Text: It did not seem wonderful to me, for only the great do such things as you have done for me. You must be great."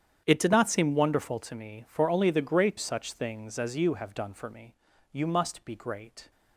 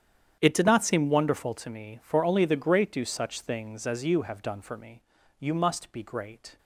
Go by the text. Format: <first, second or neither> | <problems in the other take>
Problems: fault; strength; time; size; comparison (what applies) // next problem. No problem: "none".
second | starts louder than the rest; strong; until 1.2 s; 9 dB; strong in the second // skips "do"; at 2.7 s